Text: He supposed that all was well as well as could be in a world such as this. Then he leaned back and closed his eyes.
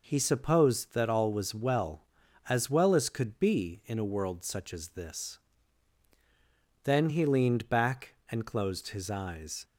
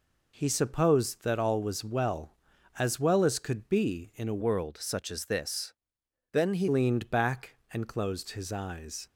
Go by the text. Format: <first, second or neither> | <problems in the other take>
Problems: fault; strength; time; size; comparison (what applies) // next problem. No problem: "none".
first | changes voice from "world" to "he"; from 4.4 to 6.6 s; 2.2 s long